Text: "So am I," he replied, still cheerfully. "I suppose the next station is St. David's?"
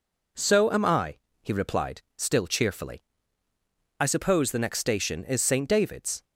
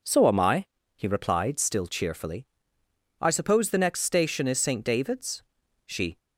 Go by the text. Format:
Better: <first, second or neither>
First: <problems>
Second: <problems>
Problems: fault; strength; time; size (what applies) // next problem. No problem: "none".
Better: first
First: none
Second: goes on to say "She"; slight; from 5.8 s on; 0.32 s long